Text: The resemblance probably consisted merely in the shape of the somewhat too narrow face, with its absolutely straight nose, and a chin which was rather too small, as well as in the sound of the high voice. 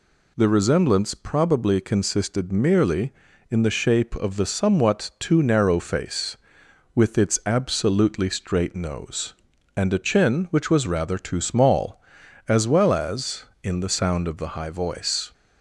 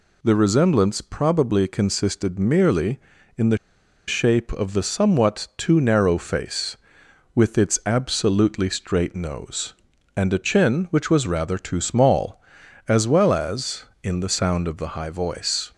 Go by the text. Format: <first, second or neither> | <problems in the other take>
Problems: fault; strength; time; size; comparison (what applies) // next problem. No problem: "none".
first | pauses between "the" and "shape"; noticeable; at 3.5 s; 0.51 s long